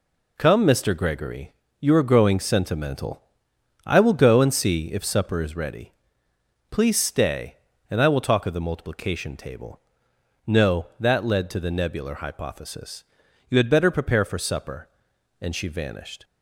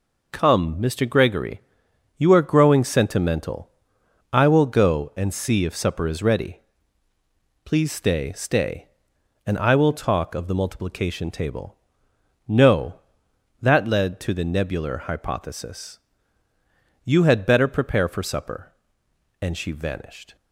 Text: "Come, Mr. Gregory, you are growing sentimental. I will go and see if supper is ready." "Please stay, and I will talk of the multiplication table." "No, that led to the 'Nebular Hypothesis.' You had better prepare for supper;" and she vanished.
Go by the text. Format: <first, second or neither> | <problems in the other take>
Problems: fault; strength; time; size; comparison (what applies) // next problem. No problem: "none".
first | says "stay" twice; at 8.3 s